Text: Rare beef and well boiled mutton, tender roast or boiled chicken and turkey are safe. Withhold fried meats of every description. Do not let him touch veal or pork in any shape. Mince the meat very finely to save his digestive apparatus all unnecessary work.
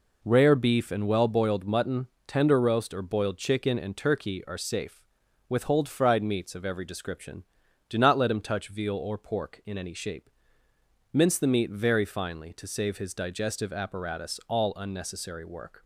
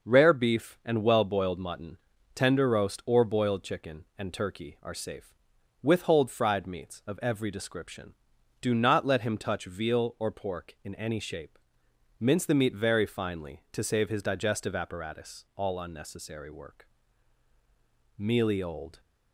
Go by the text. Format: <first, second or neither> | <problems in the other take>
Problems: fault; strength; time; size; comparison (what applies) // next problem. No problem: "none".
first | starts louder than the rest; noticeable; until 1.1 s; 6 dB // goes on to say "Mealy old"; noticeable; from 18.1 s on; 0.82 s long